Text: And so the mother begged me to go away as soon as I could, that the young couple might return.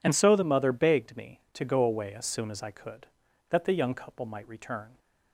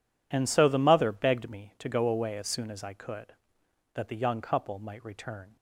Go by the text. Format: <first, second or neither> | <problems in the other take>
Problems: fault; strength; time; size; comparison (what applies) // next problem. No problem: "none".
neither | none